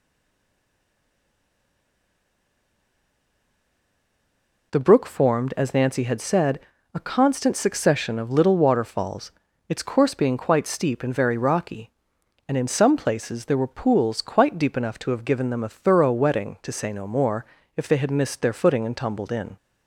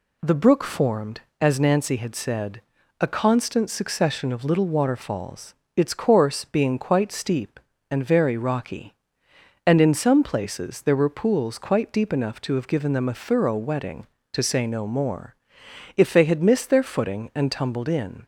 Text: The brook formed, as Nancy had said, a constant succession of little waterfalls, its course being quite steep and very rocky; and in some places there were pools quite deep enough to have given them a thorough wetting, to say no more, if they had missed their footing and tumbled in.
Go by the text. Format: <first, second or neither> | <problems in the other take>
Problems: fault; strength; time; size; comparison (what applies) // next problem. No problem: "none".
second | stays silent before the first word; strong; until 4.7 s; 4.7 s long